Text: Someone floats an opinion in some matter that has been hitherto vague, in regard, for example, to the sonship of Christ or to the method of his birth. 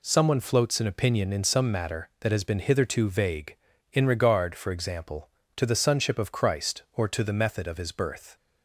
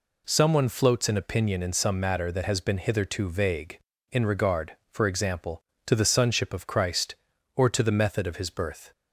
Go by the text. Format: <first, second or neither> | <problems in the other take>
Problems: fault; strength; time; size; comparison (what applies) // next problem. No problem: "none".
neither | none